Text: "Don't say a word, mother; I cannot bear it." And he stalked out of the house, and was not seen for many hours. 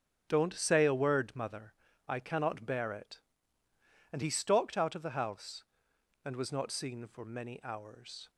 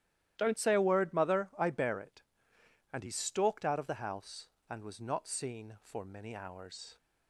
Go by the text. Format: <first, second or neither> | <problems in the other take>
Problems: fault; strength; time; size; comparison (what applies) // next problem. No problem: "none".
first | starts louder than the rest; strong; until 1.3 s; 13 dB; strong in the first // skips "cannot"; at 1.6 s